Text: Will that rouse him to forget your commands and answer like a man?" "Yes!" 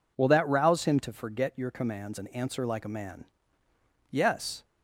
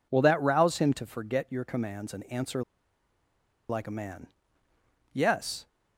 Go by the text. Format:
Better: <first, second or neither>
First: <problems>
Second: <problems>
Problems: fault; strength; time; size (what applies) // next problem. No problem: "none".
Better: first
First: none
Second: pauses between "answer" and "like"; at 2.6 s; 1.0 s long